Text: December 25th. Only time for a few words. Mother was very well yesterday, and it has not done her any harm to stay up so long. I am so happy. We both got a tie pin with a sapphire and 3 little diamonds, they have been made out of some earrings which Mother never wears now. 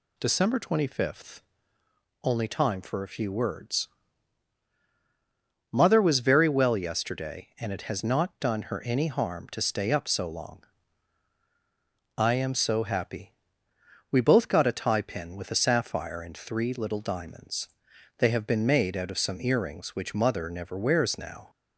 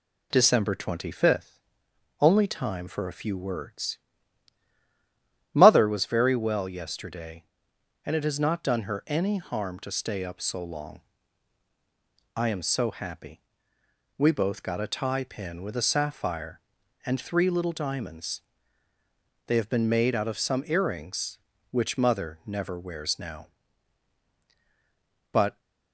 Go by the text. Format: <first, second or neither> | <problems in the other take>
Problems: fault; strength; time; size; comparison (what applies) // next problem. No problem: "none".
first | pauses between "Mother" and "never"; slight; at 22.3 s; 0.24 s long // goes on to say "But"; slight; from 25.3 s on; 0.28 s long